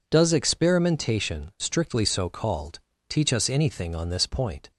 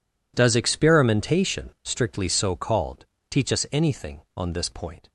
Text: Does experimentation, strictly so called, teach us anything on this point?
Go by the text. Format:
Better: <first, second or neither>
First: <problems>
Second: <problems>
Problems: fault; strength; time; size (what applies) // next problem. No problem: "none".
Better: neither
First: none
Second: none